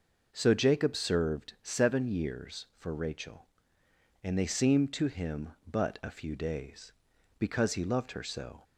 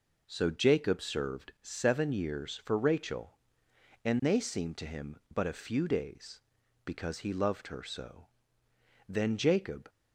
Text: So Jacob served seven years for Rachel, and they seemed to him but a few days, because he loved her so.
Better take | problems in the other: first | goes on to say "Then Jacob"; noticeable; from 9.0 s on; 0.80 s long

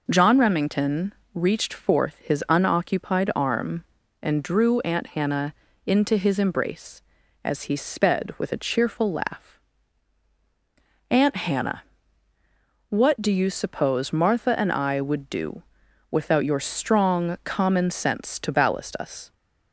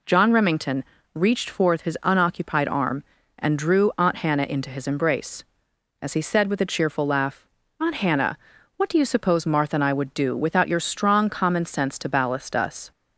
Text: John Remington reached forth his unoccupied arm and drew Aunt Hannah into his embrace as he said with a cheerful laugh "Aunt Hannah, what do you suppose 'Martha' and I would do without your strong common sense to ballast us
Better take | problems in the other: second | pauses between "Remington" and "reached"; slight; at 1.1 s; 0.22 s long; slight in the second // pauses between "Hannah" and "into"; slight; at 5.5 s; 0.32 s long // says "sped" for "said"; at 7.7 s // pauses between "laugh" and "Aunt"; strong; at 9.5 s; 1.5 s long; slight in the second // pauses between "do" and "without"; noticeable; at 15.6 s; 0.46 s long

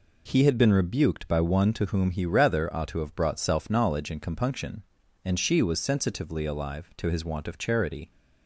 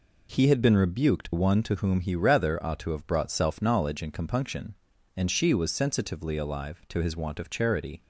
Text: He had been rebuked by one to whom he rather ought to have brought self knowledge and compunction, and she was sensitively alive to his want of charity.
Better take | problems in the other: first | skips "by"; at 1.3 s

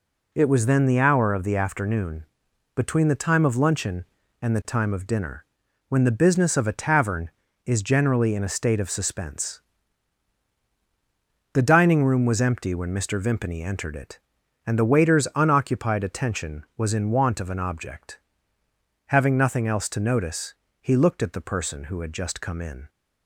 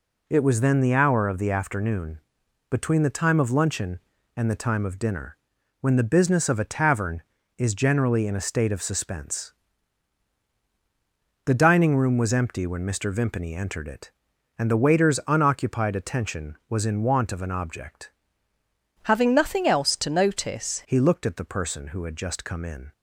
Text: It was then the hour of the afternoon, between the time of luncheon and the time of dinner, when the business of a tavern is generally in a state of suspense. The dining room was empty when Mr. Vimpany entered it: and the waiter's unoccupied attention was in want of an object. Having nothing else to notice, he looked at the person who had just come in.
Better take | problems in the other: first | changes voice from "Having" to "notice"; from 19.0 to 20.8 s; 1.8 s long

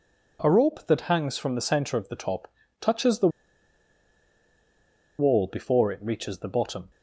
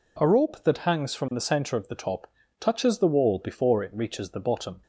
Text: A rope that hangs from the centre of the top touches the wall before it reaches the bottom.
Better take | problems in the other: second | pauses between "top" and "touches"; slight; at 2.5 s; 0.30 s long; slight in the second // pauses between "the" and "wall"; strong; at 3.2 s; 1.9 s long

